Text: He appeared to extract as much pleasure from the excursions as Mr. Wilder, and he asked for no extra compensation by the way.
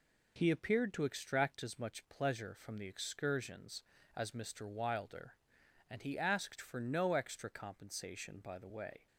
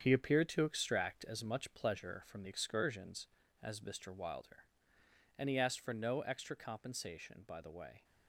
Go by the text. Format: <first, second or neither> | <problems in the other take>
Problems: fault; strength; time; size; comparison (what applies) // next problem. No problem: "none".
first | gets quieter; strong; throughout; 7.5 dB